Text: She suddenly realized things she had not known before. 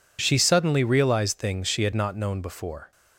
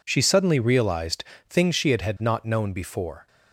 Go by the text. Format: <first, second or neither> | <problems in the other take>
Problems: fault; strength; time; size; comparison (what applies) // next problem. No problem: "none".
first | pauses between "realized" and "things"; slight; at 1.2 s; 0.24 s long // says "had" twice; at 2.0 s